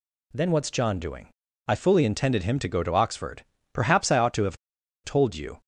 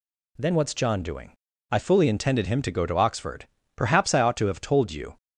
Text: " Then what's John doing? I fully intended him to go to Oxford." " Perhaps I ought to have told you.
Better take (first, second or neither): second